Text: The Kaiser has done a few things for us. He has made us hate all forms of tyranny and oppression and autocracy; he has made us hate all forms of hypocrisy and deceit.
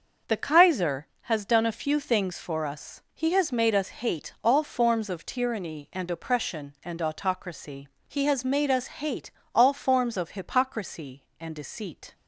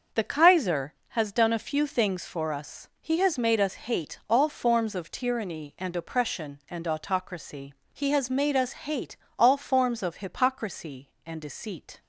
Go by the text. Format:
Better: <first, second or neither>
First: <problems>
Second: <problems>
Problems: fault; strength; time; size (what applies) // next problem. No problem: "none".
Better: neither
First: pauses between "hate" and "all"; slight; at 9.3 s; 0.24 s long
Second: pauses between "hate" and "all"; slight; at 9.1 s; 0.22 s long